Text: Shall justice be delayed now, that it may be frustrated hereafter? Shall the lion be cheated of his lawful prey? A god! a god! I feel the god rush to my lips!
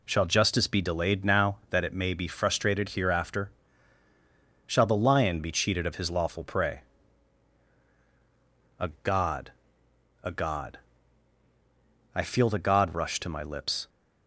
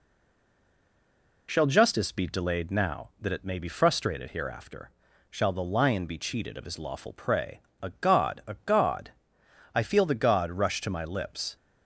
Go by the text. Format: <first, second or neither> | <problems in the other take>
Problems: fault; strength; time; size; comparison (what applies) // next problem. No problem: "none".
first | stays silent before the first word; noticeable; until 1.4 s; 1.4 s long